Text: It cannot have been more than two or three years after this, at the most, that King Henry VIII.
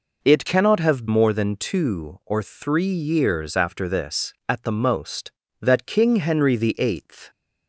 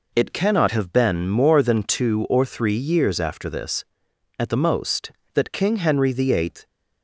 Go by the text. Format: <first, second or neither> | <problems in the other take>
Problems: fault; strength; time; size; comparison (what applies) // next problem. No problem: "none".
second | skips "been"; at 1.0 s